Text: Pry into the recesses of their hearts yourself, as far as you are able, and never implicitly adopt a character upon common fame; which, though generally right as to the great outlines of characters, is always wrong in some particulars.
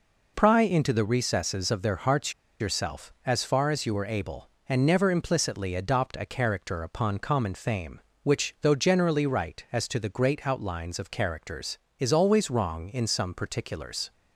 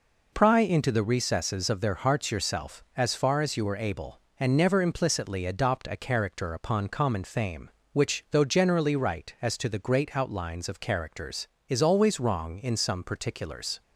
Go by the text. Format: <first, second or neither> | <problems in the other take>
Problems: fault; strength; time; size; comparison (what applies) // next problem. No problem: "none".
second | pauses between "hearts" and "yourself"; slight; at 2.3 s; 0.27 s long